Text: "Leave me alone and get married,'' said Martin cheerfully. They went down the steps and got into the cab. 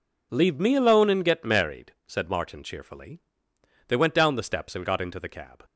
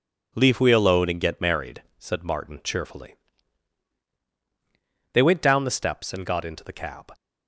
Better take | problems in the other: first | says "we" for "me"; at 0.6 s

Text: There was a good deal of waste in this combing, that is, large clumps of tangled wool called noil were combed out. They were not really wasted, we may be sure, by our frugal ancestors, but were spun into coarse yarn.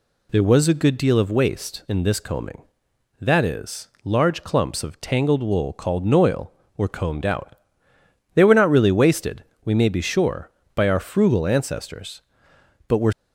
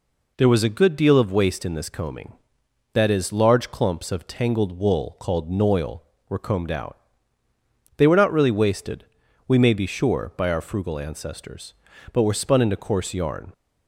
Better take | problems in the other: second | stops before "spun into coarse yarn"; at 13.1 s

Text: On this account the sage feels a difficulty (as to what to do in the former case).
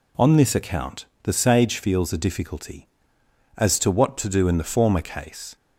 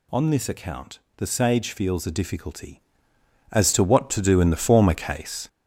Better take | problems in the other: first | gets louder; noticeable; throughout; 6 dB // pauses between "account" and "the"; slight; at 0.9 s; 0.20 s long; slight in the first

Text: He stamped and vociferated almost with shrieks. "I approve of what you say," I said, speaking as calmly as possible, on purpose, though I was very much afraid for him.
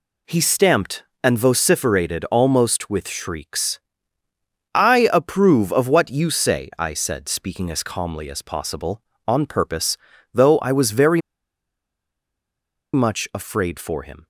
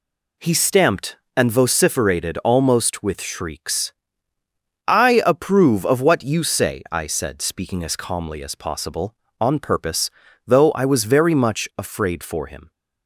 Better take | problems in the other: second | pauses between "very" and "much"; strong; at 11.2 s; 1.7 s long

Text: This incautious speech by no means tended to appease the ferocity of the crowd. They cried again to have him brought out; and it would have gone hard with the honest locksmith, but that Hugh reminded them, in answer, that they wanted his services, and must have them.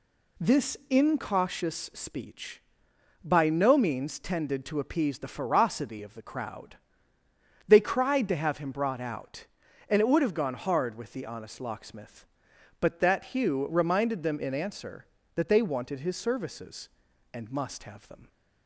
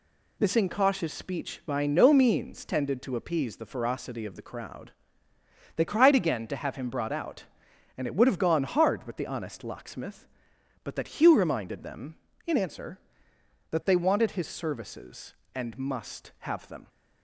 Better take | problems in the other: second | skips "again"; at 8.2 s

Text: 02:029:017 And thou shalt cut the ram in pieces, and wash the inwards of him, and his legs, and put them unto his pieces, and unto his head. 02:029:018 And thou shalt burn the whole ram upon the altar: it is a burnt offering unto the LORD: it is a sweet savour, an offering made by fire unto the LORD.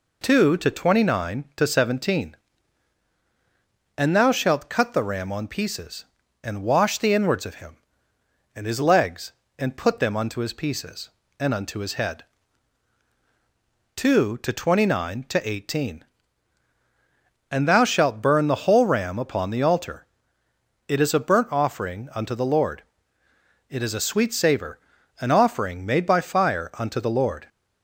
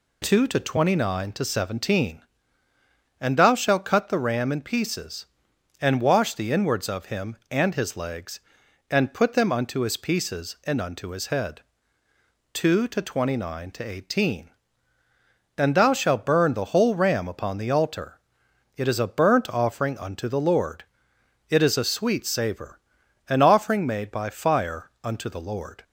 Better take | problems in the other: second | says "on" for "in"; at 5.3 s

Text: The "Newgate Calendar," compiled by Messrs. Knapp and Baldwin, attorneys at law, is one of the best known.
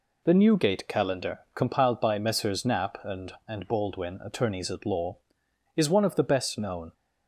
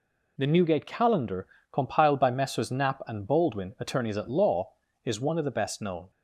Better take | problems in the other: second | says "and" twice; at 3.4 s

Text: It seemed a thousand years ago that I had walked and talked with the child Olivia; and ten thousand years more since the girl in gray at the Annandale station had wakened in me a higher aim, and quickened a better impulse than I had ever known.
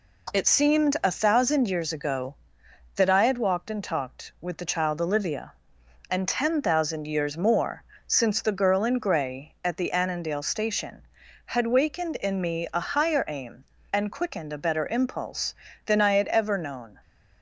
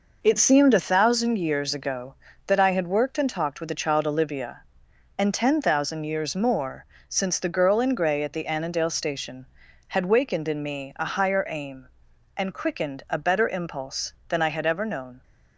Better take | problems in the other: first | says "worked" for "walked"; at 2.8 s // pauses between "more" and "since"; slight; at 6.8 s; 0.24 s long; slight in the first

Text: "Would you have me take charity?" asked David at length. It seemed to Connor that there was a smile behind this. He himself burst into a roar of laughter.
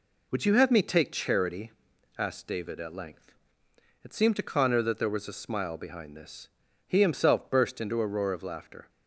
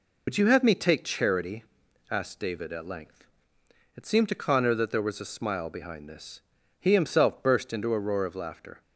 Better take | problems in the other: first | loses the start of "Would"; at 0.2 s; 45 ms

